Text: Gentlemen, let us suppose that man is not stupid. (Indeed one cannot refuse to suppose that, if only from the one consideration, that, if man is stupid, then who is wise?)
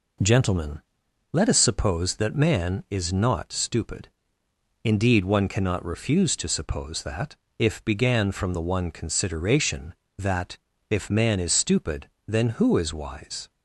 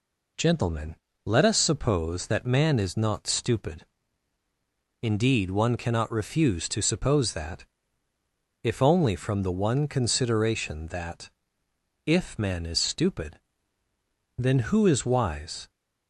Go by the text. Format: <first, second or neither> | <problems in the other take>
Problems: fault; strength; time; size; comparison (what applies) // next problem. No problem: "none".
second | says "began" for "only"; at 7.8 s